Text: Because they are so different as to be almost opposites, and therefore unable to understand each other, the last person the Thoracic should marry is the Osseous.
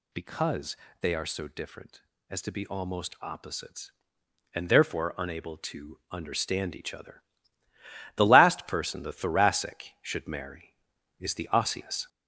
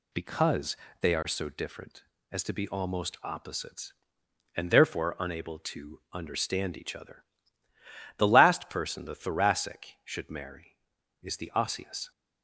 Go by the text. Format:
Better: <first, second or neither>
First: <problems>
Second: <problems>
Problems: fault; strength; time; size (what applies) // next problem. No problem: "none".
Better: second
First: gets louder; throughout; 3.5 dB // pauses between "Because" and "they"; slight; at 0.7 s; 0.24 s long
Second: pauses between "Because" and "they"; slight; at 0.7 s; 0.24 s long